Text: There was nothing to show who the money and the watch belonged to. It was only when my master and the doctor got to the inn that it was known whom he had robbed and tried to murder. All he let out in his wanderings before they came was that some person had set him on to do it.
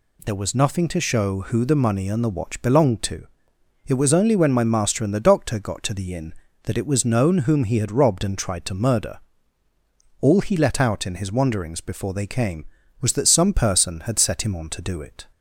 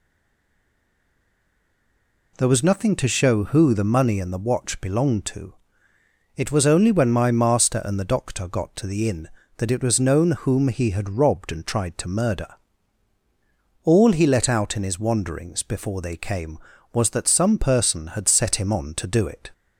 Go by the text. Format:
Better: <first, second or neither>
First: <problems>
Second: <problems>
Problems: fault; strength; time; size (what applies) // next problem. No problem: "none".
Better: first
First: none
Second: stays silent before the first word; until 2.3 s; 2.3 s long